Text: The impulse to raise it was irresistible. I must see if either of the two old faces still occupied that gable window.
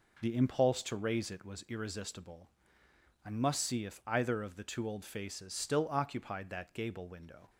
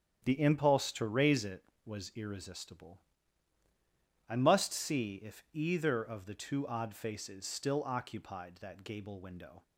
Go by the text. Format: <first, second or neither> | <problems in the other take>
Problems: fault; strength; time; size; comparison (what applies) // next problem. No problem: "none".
first | starts louder than the rest; strong; until 1.2 s; 8.5 dB // says "odd" for "old"; at 6.6 s